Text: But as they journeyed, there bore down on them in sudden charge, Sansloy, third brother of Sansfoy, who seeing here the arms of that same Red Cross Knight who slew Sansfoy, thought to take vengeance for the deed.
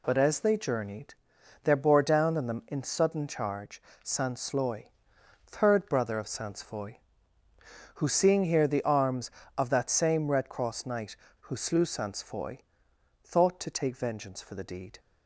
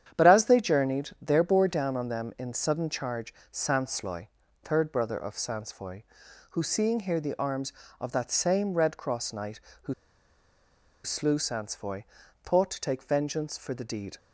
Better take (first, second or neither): first